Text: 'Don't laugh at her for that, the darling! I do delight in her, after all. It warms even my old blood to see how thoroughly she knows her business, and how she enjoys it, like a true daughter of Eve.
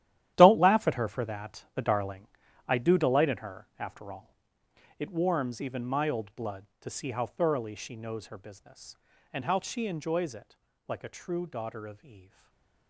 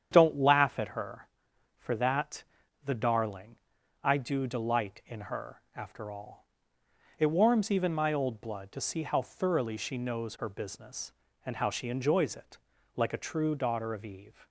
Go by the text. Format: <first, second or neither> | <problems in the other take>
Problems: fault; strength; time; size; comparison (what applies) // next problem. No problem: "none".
second | gets quieter; strong; throughout; 14 dB // starts louder than the rest; strong; until 1.3 s; 12.5 dB; strong in the second // stays silent after the last word; slight; from 12.2 s on; 0.6 s long